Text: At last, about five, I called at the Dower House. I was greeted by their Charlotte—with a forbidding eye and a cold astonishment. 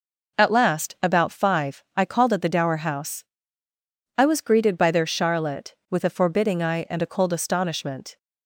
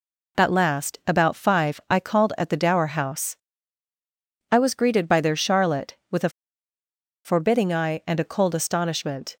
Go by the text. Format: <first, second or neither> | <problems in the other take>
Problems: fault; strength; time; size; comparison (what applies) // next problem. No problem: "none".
first | pauses between "a" and "forbidding"; noticeable; at 6.2 s; 0.96 s long